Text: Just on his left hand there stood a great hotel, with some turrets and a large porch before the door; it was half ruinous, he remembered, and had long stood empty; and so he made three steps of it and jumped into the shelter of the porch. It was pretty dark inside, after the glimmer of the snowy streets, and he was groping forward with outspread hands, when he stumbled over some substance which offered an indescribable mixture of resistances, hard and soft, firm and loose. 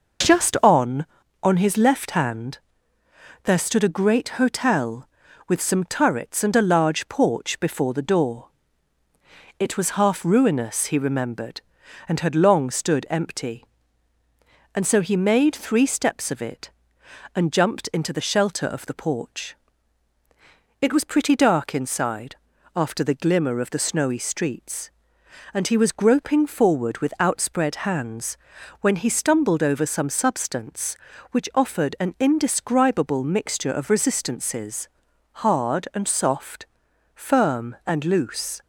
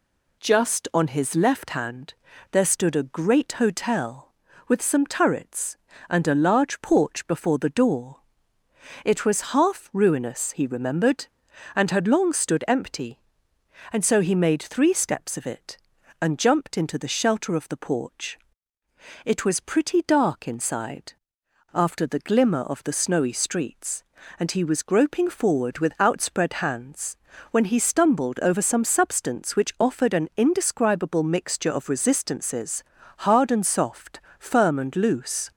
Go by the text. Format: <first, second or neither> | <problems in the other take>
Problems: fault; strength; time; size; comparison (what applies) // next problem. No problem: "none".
second | says "on" twice; at 1.4 s // pauses between "hand" and "there"; noticeable; at 2.5 s; 0.86 s long; also in the second